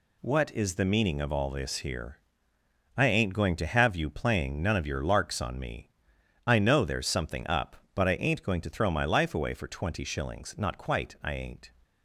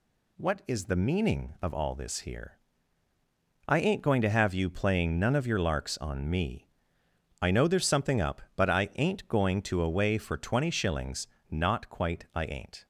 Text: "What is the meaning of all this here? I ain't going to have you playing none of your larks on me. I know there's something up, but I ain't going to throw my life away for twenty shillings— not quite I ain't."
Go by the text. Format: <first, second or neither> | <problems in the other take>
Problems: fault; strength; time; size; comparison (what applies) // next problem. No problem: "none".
first | skips "throw my life"; at 9.8 s